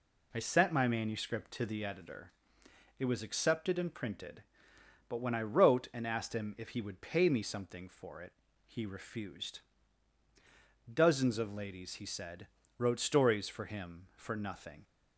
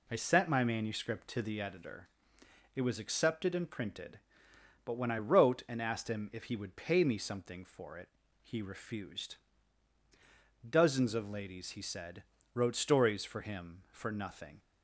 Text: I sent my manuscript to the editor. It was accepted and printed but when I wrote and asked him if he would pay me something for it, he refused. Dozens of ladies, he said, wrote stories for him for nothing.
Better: neither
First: none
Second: none

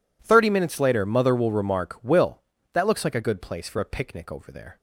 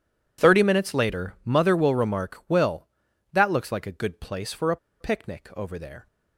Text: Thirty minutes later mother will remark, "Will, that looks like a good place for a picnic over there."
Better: first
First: none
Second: pauses between "a" and "picnic"; slight; at 4.7 s; 0.23 s long

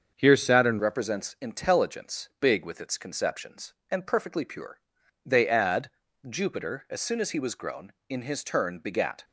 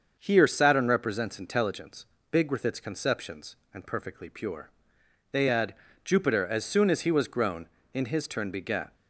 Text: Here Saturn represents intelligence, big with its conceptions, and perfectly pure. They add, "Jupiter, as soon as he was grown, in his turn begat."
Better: second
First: starts louder than the rest; until 1.1 s; 7 dB // changes voice at "represents"; from 0.7 s on; 8.5 s long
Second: starts louder than the rest; until 1.2 s; 6.5 dB

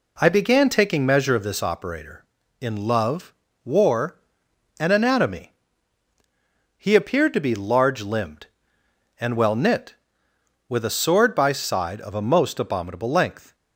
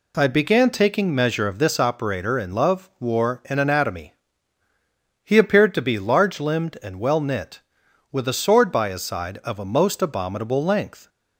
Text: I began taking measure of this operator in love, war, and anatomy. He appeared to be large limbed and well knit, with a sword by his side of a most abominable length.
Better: second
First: skips "his"; at 11.5 s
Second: none

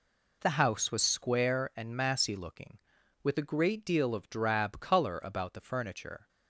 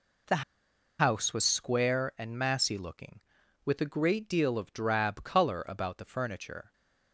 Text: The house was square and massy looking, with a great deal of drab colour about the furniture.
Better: first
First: none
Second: pauses between "The" and "house"; noticeable; at 0.4 s; 0.58 s long

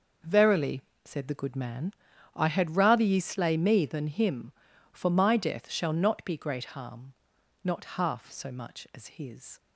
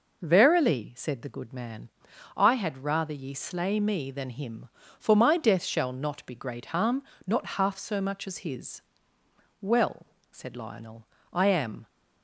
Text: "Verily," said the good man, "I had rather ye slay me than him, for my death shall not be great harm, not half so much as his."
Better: first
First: none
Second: goes on to say "Well said Lionel I am"; strong; from 9.6 s on; 2.2 s long

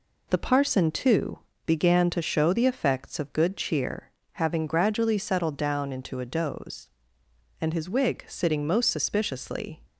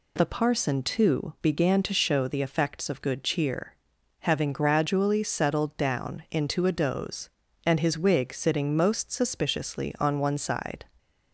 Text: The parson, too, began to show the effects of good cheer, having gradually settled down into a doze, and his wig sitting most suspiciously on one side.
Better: second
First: stops before "on one side"; at 9.8 s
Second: none

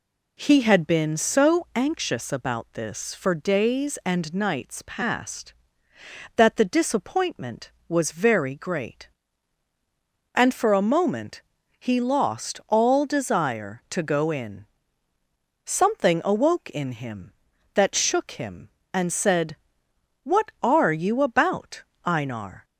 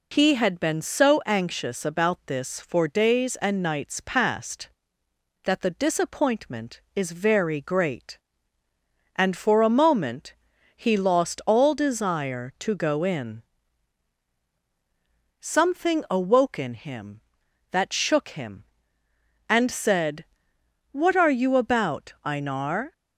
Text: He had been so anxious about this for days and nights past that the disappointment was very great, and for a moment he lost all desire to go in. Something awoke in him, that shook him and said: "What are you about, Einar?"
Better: first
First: pauses between "moment" and "he"; at 11.4 s; 0.38 s long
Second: says "is" for "was"; at 6.9 s // pauses between "moment" and "he"; at 10.3 s; 0.42 s long

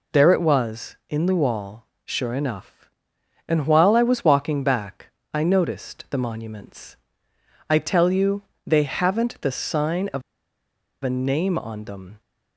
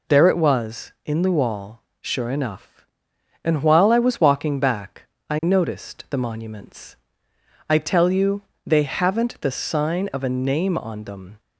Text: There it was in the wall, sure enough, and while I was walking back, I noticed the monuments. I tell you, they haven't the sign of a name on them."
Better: second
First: pauses between "of" and "a"; noticeable; at 10.2 s; 0.82 s long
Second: none

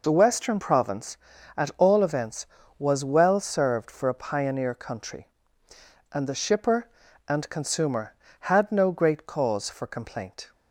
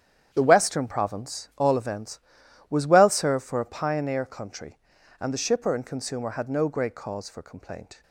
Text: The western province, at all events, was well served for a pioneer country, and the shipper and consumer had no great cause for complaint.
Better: first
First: none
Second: starts louder than the rest; strong; until 1.3 s; 9 dB // skips "at"; at 1.5 s

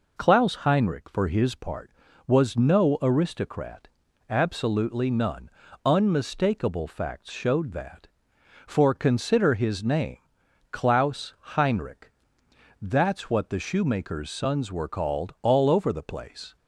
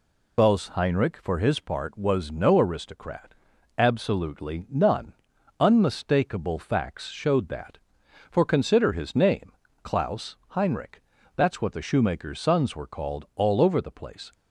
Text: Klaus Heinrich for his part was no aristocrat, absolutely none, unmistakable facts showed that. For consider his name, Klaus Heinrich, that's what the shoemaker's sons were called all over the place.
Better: first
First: none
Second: loses the start of "Klaus"; at 0.3 s; 40 ms

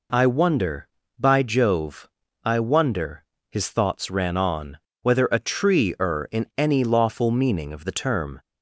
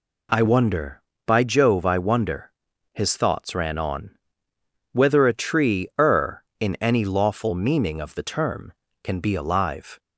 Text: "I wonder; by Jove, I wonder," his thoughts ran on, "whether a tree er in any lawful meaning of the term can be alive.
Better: second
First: stops before "can be alive"; at 8.3 s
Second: none

